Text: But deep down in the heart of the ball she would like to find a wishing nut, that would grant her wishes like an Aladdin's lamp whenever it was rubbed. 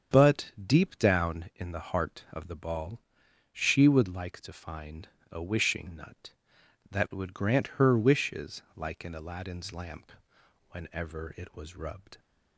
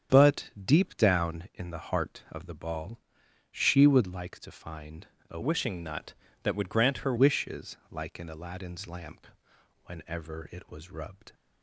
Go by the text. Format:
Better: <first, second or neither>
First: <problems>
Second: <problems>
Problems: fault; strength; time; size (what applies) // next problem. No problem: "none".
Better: first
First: starts louder than the rest; strong; until 1.2 s; 7.5 dB // pauses between "ball" and "she"; noticeable; at 3.0 s; 0.50 s long // pauses between "find" and "a"; slight; at 5.0 s; 0.22 s long // pauses between "wishes" and "like"; slight; at 8.6 s; 0.16 s long // pauses between "lamp" and "whenever"; noticeable; at 10.1 s; 0.56 s long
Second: starts louder than the rest; strong; until 1.2 s; 8 dB // pauses between "ball" and "she"; noticeable; at 2.9 s; 0.50 s long // pauses between "find" and "a"; slight; at 5.0 s; 0.22 s long // changes voice from "wishing" to "her"; from 5.4 to 7.1 s; 1.7 s long // pauses between "wishes" and "like"; slight; at 7.7 s; 0.16 s long // pauses between "lamp" and "whenever"; noticeable; at 9.2 s; 0.56 s long